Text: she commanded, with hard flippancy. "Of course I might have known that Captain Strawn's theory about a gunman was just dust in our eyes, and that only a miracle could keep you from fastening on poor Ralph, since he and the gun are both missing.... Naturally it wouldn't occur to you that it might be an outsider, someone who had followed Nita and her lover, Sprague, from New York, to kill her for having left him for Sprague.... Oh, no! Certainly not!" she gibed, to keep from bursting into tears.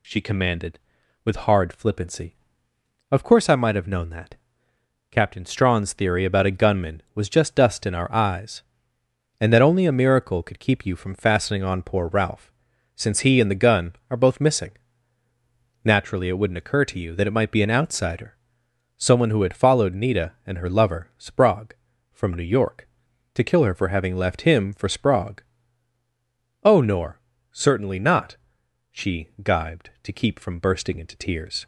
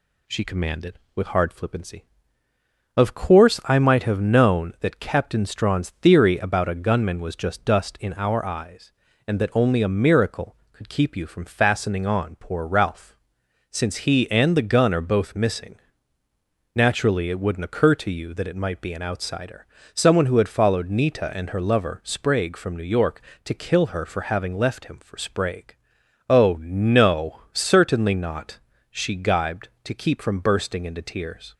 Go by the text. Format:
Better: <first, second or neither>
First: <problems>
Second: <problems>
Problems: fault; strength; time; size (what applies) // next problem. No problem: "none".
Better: second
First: pauses between "that" and "Captain"; noticeable; at 4.3 s; 0.74 s long // says "nor" for "no"; at 26.7 s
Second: none